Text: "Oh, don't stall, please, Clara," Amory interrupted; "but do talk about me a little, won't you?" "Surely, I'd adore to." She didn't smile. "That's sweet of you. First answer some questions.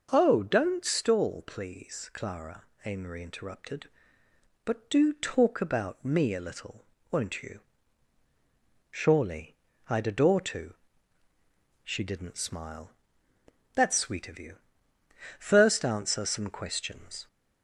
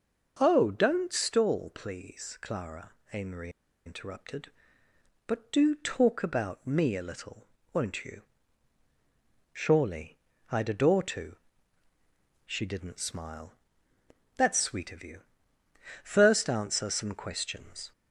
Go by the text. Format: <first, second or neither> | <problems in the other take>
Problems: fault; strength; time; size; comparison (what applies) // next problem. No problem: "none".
first | pauses between "Amory" and "interrupted"; at 3.4 s; 0.36 s long